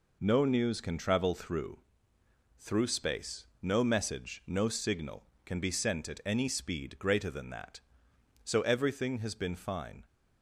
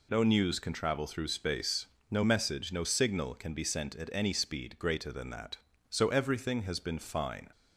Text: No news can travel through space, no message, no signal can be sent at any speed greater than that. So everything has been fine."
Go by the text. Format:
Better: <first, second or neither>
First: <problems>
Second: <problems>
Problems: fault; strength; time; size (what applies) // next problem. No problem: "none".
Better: second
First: says "through" twice; at 2.5 s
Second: none